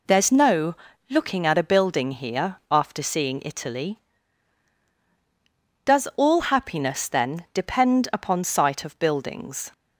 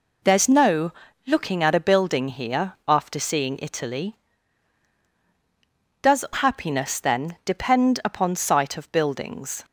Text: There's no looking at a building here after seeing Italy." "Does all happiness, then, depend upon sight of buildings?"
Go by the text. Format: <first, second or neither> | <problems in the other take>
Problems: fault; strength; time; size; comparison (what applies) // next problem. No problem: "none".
first | pauses between "no" and "looking"; slight; at 0.9 s; 0.36 s long; slight in the first // skips "all"; at 6.2 s